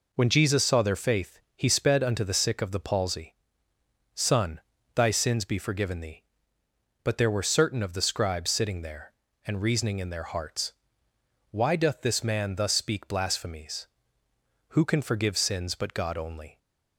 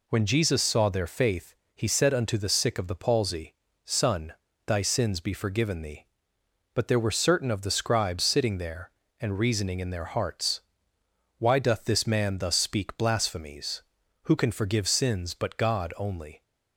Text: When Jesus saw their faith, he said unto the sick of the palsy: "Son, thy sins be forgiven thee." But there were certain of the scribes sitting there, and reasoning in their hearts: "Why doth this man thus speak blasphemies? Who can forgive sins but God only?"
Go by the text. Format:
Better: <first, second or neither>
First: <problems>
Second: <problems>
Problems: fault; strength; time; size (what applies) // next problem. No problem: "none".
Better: second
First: says "sped" for "said"; at 1.7 s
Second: none